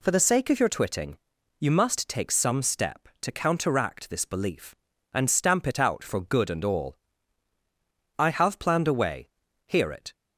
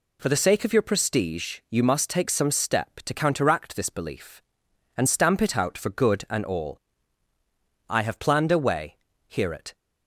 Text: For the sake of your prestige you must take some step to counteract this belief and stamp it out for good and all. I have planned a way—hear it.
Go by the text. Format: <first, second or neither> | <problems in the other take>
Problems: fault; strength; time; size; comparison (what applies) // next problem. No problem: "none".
second | says "twitting" for "prestige"; at 0.6 s